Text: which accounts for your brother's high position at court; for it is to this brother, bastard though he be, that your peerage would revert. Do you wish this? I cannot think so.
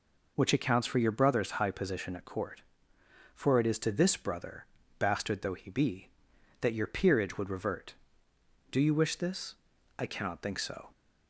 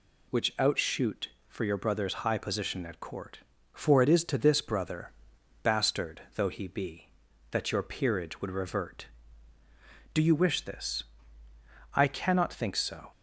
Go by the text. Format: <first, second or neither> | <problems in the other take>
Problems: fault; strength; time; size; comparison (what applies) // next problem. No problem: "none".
first | says "outshoot" for "accounts"; at 0.5 s